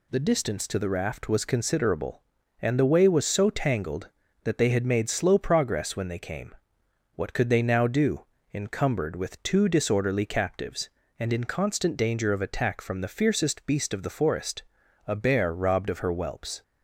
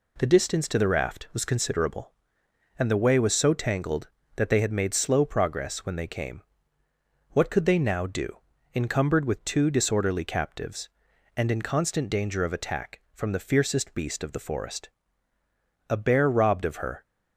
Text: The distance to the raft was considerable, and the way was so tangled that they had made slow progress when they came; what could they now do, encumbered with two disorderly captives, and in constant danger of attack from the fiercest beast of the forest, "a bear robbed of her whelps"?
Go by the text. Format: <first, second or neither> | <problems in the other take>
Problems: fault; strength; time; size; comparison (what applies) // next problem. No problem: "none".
first | stops before "whelps"; at 17.0 s